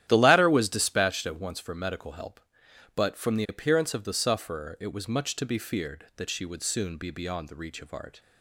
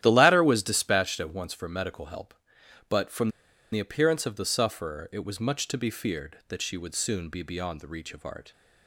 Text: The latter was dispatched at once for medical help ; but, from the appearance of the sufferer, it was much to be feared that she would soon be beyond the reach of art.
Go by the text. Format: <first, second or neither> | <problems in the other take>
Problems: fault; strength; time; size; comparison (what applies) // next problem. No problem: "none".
first | starts louder than the rest; strong; until 1.0 s; 11.5 dB; strong in the first // pauses between "from" and "the"; at 3.2 s; 0.43 s long